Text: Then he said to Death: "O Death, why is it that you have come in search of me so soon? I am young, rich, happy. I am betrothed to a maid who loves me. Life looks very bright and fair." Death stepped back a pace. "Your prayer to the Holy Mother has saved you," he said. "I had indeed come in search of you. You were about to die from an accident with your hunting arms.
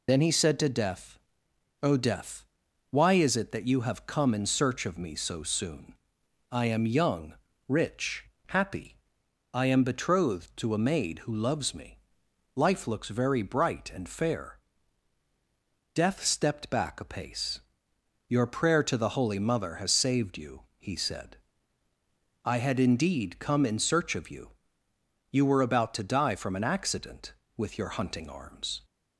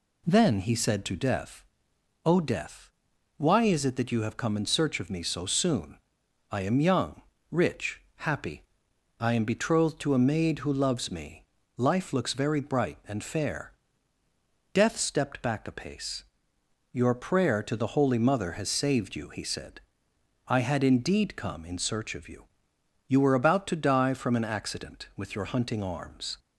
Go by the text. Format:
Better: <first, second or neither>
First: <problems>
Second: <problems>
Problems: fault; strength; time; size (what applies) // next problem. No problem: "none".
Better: second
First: loses the start of "Then"; at 0.0 s; 50 ms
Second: none